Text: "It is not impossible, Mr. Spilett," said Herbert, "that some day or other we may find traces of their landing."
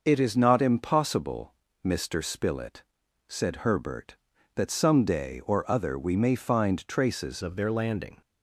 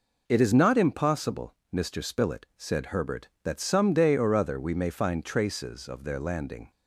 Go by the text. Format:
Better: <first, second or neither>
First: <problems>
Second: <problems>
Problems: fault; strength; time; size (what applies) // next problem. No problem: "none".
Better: second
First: changes voice at "of"; from 7.4 s on; 0.8 s long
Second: none